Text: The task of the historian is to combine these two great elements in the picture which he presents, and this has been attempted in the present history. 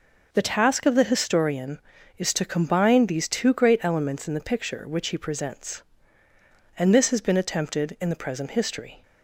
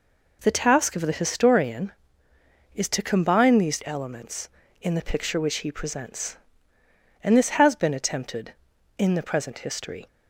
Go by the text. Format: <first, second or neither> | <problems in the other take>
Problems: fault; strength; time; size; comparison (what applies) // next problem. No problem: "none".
first | skips "two great"; at 3.8 s